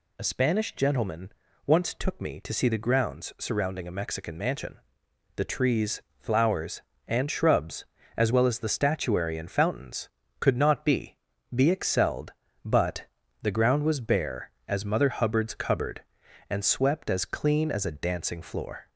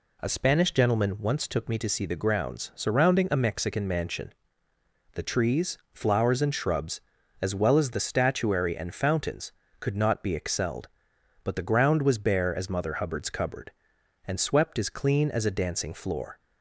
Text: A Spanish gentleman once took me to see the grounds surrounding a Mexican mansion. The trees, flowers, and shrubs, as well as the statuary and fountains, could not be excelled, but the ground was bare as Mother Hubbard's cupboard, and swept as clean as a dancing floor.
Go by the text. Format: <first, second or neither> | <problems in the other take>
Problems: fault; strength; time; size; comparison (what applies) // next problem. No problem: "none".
second | pauses between "gentleman" and "once"; slight; at 1.3 s; 0.34 s long // says "be" twice; at 11.5 s // pauses between "but" and "the"; slight; at 13.0 s; 0.36 s long